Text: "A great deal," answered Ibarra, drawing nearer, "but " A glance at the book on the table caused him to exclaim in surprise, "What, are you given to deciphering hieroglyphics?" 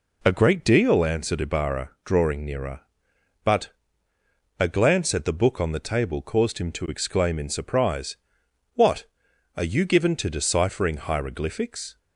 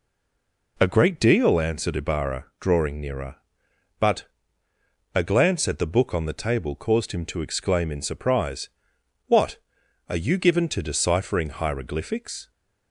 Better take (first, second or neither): first